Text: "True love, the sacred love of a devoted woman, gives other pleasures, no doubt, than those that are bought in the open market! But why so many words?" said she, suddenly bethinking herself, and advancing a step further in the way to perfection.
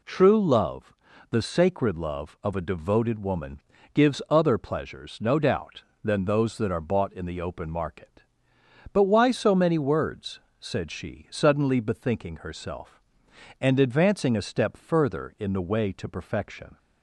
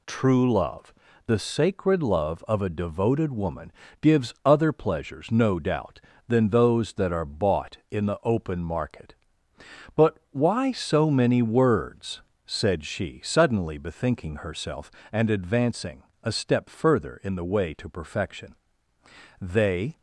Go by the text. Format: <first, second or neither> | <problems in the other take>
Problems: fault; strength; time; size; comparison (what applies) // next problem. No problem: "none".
first | pauses between "advancing" and "a"; slight; at 16.0 s; 0.20 s long // goes on to say "They"; from 19.4 s on; 0.58 s long